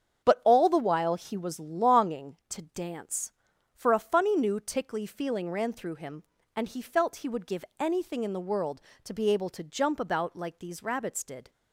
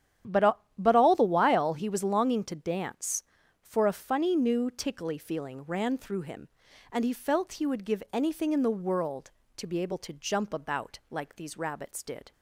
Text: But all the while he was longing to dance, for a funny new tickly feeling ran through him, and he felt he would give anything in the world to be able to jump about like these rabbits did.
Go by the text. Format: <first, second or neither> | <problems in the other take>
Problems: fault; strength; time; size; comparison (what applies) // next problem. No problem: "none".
first | starts louder than the rest; strong; until 1.4 s; 10 dB; strong in the first // says "But" twice; at 0.7 s